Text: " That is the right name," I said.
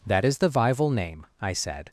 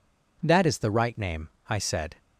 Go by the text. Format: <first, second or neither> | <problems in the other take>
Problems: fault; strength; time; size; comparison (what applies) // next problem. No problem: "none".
second | says "vival" for "right"; at 0.4 s